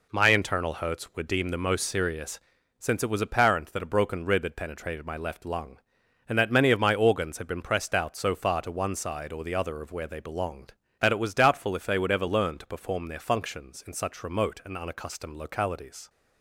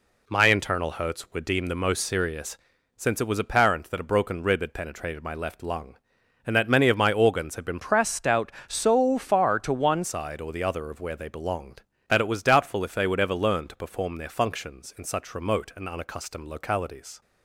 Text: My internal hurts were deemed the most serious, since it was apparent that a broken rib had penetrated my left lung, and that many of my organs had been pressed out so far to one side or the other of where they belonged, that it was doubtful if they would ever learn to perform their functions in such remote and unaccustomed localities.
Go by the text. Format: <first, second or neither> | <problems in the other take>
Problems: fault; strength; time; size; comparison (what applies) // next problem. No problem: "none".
first | changes voice from "pressed" to "one"; from 7.7 to 10.0 s; 2.3 s long